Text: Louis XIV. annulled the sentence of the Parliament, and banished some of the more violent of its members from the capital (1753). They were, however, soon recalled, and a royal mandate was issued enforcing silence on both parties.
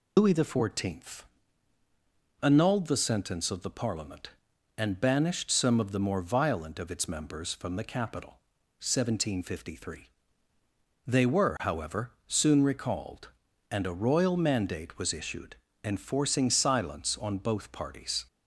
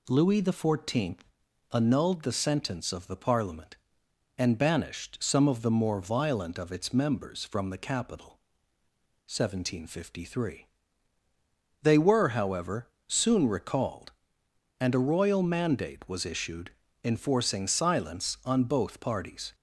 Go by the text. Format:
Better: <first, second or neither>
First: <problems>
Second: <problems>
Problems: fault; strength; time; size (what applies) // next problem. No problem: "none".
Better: second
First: loses the start of "Louis"; at 0.1 s; 125 ms // pauses between "issued" and "enforcing"; slight; at 15.5 s; 0.28 s long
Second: pauses between "issued" and "enforcing"; slight; at 16.6 s; 0.34 s long